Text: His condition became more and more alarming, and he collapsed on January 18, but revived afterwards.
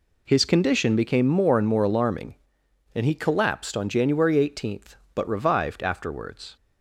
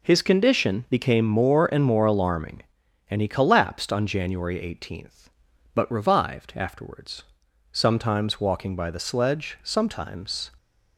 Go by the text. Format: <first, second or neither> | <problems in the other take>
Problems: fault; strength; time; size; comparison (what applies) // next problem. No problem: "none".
first | goes on to say "Sometimes walking by the sledge sometimes"; strong; from 7.7 s on; 2.7 s long